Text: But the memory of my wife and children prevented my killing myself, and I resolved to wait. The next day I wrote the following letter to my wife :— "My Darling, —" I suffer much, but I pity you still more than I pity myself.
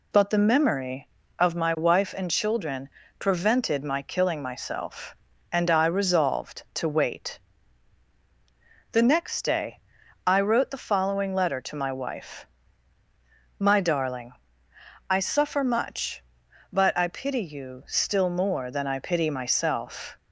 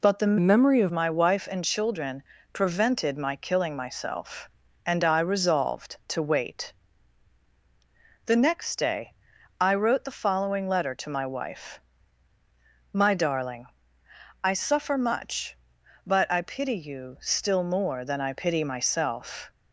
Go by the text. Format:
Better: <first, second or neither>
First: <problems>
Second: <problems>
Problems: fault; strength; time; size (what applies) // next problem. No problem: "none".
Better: first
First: pauses between "children" and "prevented"; slight; at 2.8 s; 0.30 s long // pauses between "day" and "I"; at 9.8 s; 0.44 s long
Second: changes voice from "memory" to "of"; from 0.3 to 0.9 s; 0.6 s long // pauses between "children" and "prevented"; slight; at 2.2 s; 0.30 s long // pauses between "day" and "I"; at 9.1 s; 0.44 s long